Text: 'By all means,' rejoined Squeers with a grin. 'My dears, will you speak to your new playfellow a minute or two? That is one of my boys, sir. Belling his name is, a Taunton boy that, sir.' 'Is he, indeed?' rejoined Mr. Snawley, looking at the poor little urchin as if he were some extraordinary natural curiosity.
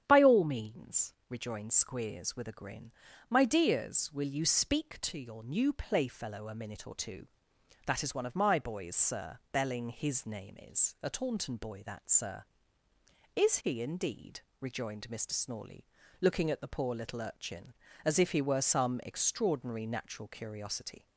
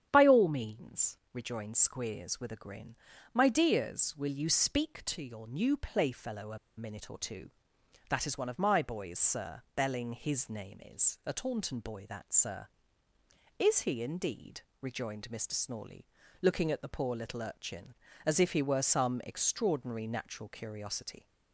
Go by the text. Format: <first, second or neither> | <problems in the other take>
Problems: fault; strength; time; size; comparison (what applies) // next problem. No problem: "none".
first | starts louder than the rest; strong; until 1.1 s; 9 dB; strong in the first // pauses between "a" and "minute"; slight; at 6.5 s; 0.20 s long